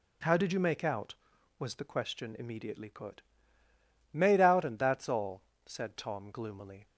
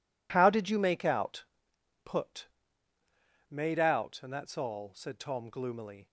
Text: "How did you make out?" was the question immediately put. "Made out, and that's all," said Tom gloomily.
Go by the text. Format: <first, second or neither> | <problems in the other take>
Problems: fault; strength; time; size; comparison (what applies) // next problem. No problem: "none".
first | skips "was the question immediately"; at 1.7 s